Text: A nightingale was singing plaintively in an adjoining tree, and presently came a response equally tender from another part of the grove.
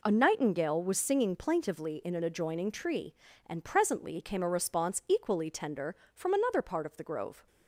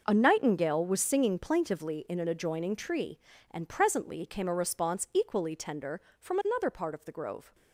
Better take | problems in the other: first | gets quieter; strong; throughout; 13 dB

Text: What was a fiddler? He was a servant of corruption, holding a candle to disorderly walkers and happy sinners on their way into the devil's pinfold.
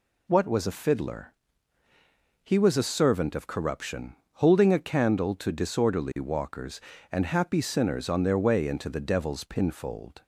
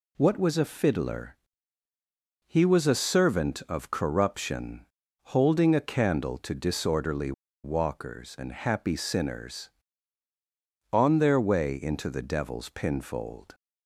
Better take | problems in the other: first | pauses between "disorderly" and "walkers"; slight; at 7.3 s; 0.30 s long

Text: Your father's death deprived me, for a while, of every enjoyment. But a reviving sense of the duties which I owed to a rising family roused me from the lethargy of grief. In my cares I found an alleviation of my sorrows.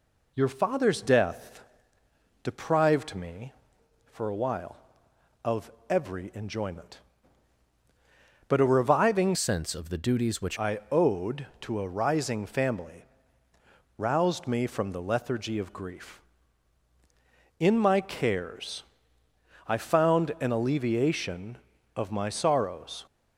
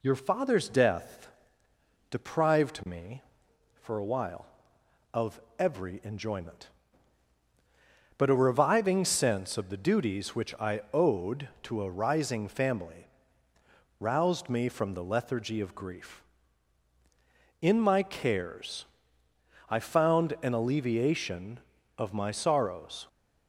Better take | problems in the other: second | pauses between "death" and "deprived"; noticeable; at 1.6 s; 0.80 s long; noticeable in the second // pauses between "of" and "every"; slight; at 5.6 s; 0.20 s long; slight in the second // changes voice from "sense" to "which"; from 9.3 to 10.5 s; 1.2 s long // pauses between "family" and "roused"; noticeable; at 13.0 s; 0.92 s long; noticeable in the second // pauses between "cares" and "I"; noticeable; at 18.8 s; 0.84 s long; noticeable in the second

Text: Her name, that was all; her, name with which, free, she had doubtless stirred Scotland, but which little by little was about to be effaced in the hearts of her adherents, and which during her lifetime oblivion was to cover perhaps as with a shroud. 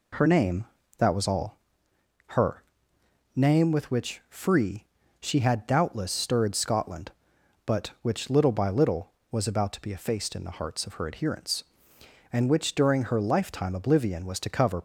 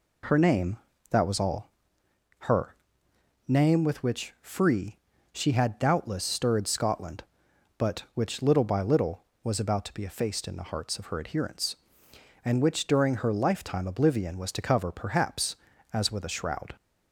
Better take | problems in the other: second | stops before "perhaps as with a shroud"; at 14.7 s

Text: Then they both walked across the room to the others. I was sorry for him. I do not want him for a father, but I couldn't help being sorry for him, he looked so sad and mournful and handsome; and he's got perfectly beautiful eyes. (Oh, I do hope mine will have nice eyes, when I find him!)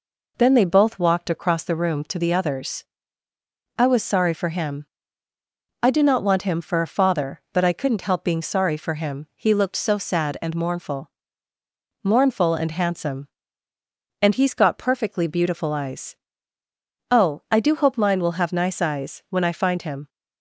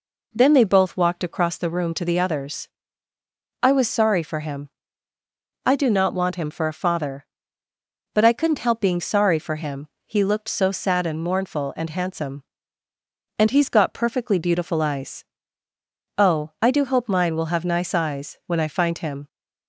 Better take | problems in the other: second | says "mournful" twice; at 12.0 s

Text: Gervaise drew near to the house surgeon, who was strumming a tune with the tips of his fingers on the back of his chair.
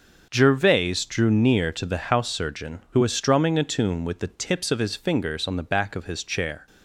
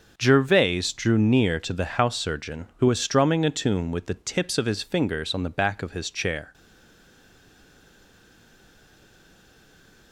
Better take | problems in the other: first | starts louder than the rest; until 1.1 s; 6 dB; also in the first // stays silent after the last word; strong; from 6.5 s on; 3.6 s long

